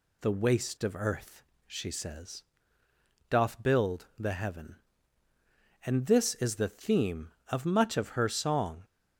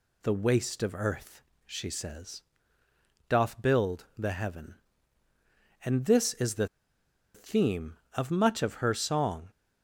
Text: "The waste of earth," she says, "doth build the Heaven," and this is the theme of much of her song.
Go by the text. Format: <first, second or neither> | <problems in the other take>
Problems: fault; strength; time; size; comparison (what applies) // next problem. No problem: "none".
first | pauses between "the" and "theme"; noticeable; at 6.6 s; 0.67 s long